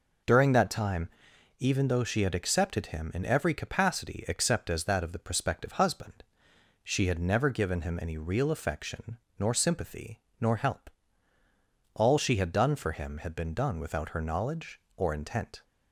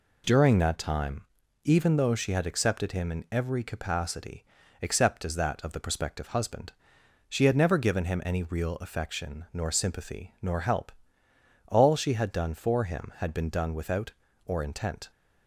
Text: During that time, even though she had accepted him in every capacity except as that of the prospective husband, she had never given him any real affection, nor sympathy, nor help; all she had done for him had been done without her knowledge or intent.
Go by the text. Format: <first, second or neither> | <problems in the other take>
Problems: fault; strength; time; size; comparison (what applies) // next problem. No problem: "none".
first | pauses between "capacity" and "except"; at 4.4 s; 0.38 s long // skips "her knowledge"; at 14.2 s